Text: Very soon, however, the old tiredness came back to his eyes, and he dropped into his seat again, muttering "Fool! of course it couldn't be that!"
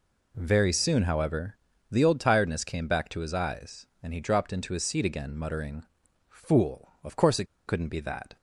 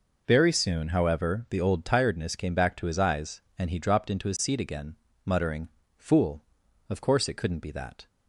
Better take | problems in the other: second | pauses between "muttering" and "Fool"; at 5.8 s; 0.42 s long; slight in the second // pauses between "it" and "couldn't"; slight; at 7.4 s; 0.21 s long

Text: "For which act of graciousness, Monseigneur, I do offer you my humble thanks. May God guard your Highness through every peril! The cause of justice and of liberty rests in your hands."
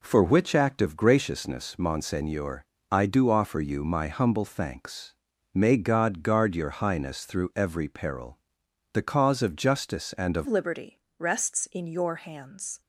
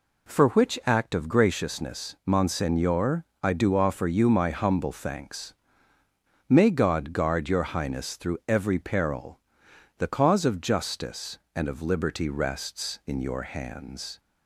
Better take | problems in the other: second | changes voice at "liberty"; from 10.4 s on; 2.4 s long // pauses between "liberty" and "rests"; slight; at 11.0 s; 0.16 s long

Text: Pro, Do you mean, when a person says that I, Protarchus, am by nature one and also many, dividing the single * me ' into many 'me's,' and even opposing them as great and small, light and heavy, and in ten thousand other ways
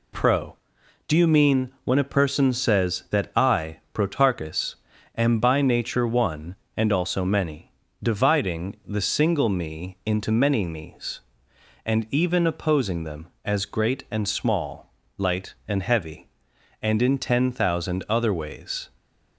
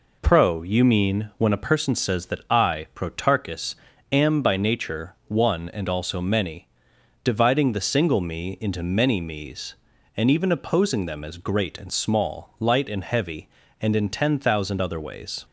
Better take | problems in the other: first | skips "Do"; at 0.6 s

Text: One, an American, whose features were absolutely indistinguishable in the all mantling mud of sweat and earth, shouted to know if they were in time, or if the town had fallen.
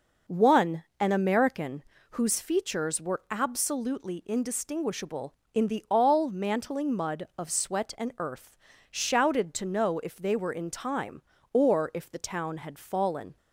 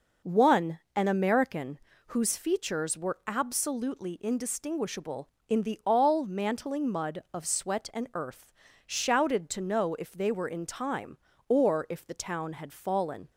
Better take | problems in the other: neither | none

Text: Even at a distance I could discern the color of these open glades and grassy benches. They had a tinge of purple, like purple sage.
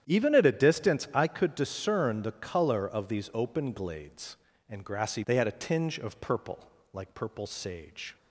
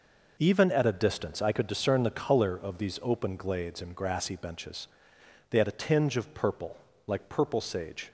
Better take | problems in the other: second | starts louder than the rest; strong; until 1.0 s; 10 dB // skips "benches"; at 5.2 s

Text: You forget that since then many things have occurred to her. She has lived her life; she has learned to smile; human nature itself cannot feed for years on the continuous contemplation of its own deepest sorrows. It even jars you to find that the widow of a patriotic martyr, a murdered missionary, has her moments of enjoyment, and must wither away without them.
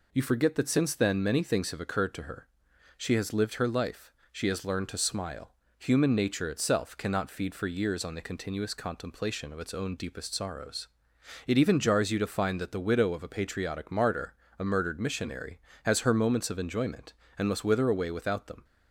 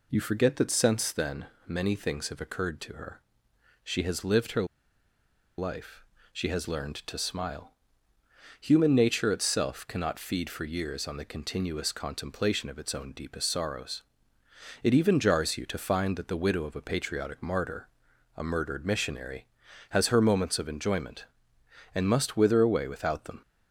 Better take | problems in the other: first | pauses between "then" and "many"; slight; at 1.4 s; 0.22 s long // pauses between "her" and "life"; noticeable; at 4.6 s; 0.93 s long

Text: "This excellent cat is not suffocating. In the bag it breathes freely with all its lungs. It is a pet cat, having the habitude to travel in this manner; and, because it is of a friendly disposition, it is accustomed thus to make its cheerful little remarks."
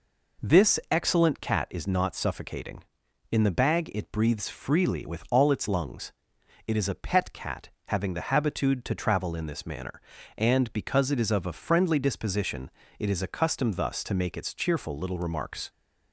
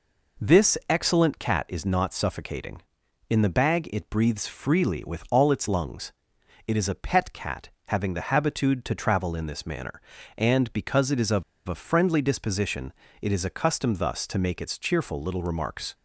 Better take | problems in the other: first | pauses between "of" and "a"; slight; at 11.4 s; 0.23 s long

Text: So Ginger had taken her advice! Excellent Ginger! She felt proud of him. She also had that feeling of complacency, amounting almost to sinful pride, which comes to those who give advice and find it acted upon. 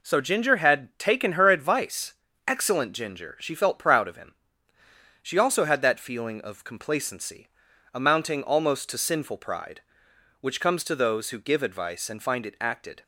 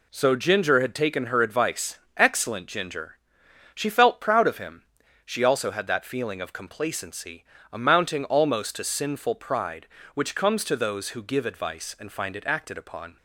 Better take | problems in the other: second | stops before "upon"; at 13.0 s

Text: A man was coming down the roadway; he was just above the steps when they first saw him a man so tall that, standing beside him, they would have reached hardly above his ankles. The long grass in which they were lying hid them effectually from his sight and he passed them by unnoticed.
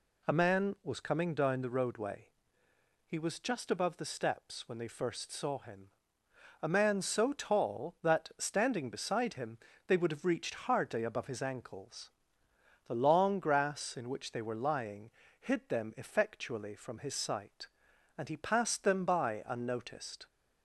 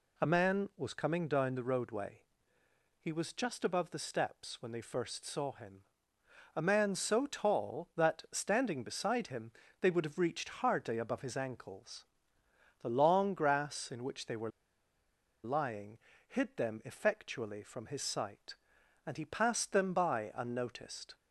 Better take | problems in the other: first | pauses between "him" and "a"; noticeable; at 5.8 s; 0.74 s long; noticeable in the first // pauses between "were" and "lying"; noticeable; at 14.4 s; 0.95 s long // pauses between "lying" and "hid"; slight; at 15.9 s; 0.30 s long; slight in the first

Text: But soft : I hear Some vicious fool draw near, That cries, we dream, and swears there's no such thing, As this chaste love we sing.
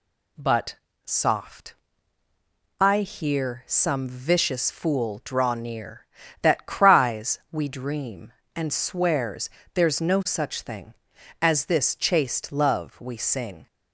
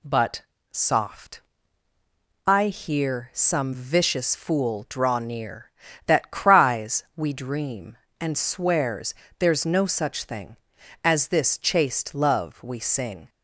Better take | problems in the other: neither | pauses between "But" and "soft"; slight; the same in both // pauses between "swears" and "there's"; slight; the same in both

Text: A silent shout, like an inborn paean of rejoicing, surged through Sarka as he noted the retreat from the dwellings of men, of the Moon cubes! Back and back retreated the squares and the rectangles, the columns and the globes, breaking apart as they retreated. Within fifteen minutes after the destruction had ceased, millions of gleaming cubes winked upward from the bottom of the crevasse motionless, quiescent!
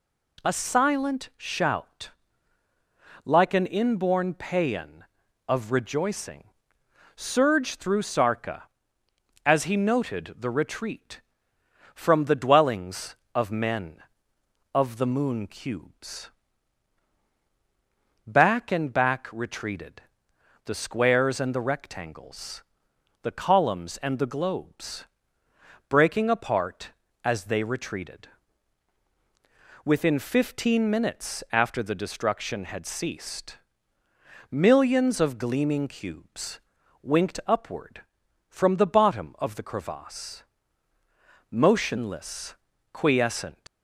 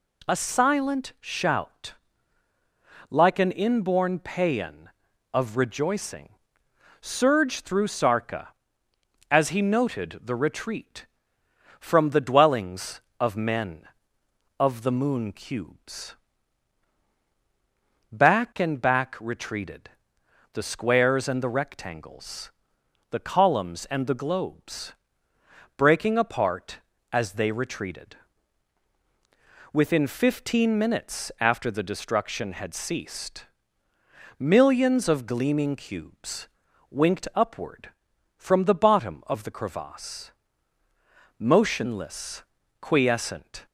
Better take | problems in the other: second | pauses between "retreated" and "the"; noticeable; at 20.0 s; 0.64 s long; noticeable in the second // pauses between "cubes" and "winked"; at 36.5 s; 0.42 s long; also in the second // pauses between "crevasse" and "motionless"; at 40.4 s; 1.0 s long; also in the second // leaves "quiescent" unfinished; at 43.6 s; 105 ms

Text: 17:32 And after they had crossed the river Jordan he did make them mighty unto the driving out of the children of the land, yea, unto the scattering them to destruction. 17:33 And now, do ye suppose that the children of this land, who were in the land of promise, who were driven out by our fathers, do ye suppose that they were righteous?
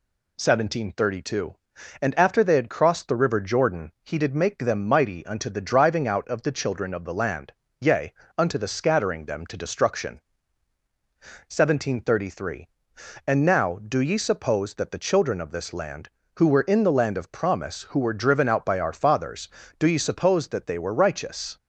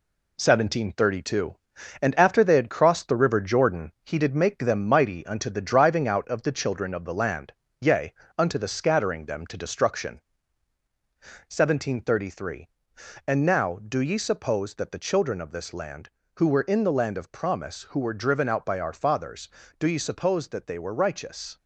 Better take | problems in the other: first | gets quieter; noticeable; throughout; 5 dB

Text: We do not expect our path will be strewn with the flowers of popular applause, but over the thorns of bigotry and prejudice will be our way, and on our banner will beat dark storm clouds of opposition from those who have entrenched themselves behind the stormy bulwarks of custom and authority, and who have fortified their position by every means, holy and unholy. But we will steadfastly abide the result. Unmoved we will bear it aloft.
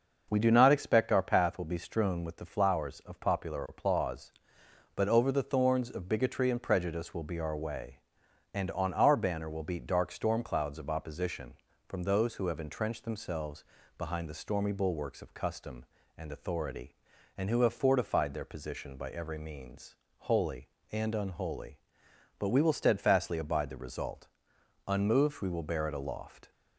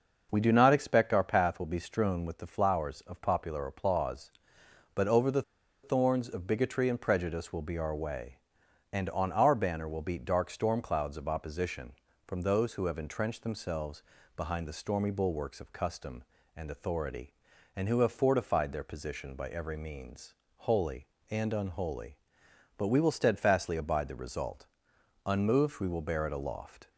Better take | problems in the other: first | starts louder than the rest; noticeable; until 1.3 s; 6 dB; noticeable in the first // pauses between "the" and "thorns"; at 5.4 s; 0.41 s long // pauses between "themselves" and "behind"; slight; at 14.0 s; 0.32 s long; slight in the first

